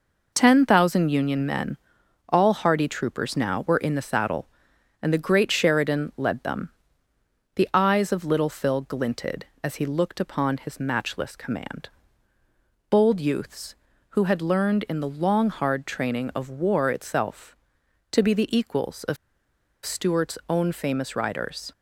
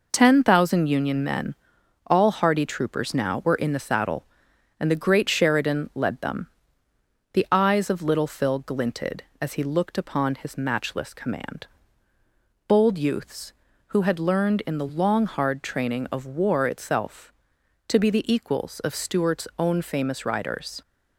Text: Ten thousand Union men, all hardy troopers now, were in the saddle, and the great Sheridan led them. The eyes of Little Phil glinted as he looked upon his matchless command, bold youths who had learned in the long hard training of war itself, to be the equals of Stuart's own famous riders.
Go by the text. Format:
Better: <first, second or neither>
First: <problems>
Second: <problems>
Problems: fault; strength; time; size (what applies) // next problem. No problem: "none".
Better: second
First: pauses between "of" and "Stuart's"; noticeable; at 19.1 s; 0.68 s long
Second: none